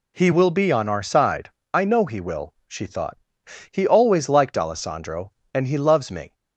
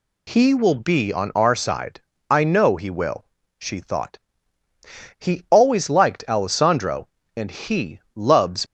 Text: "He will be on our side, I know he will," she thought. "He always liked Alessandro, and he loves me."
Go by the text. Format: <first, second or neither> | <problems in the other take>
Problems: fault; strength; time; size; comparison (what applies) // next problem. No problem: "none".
first | stops before "me"; at 8.6 s